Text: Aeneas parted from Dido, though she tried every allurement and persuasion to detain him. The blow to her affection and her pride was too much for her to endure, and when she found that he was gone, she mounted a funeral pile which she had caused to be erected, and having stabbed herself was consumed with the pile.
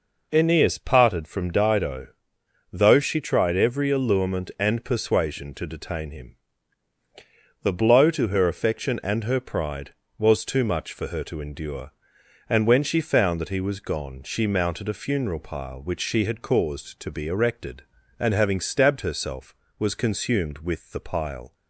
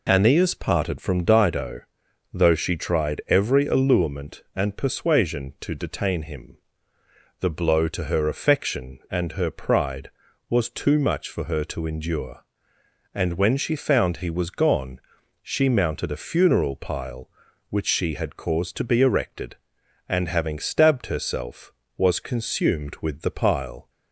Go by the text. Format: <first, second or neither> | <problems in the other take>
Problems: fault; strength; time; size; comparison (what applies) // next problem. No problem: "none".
first | skips "that"; at 14.1 s